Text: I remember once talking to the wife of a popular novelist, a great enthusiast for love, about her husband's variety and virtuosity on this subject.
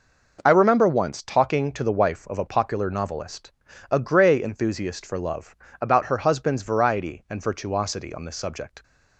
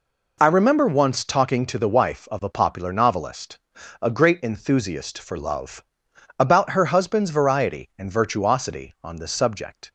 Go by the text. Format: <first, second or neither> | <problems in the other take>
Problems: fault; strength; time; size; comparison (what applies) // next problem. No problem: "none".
second | says "grey" for "great"; at 3.9 s